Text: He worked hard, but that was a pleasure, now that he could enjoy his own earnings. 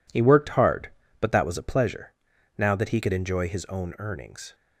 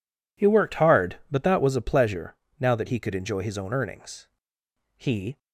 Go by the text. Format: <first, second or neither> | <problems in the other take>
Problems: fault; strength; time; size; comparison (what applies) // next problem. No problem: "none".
first | goes on to say "He"; slight; from 4.9 s on; 0.40 s long